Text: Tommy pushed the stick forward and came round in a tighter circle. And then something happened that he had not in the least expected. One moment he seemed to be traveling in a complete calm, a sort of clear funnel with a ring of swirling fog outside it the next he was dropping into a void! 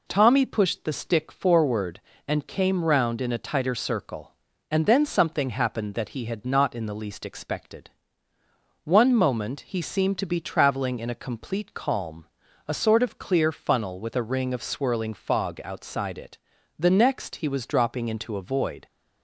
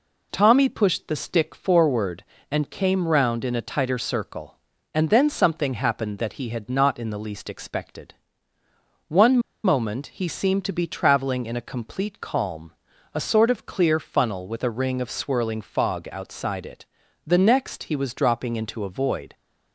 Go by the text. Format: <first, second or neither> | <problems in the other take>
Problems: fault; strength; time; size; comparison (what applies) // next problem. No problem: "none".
first | pauses between "One" and "moment"; slight; at 9.3 s; 0.25 s long // pauses between "it" and "the"; at 16.8 s; 0.40 s long; also in the first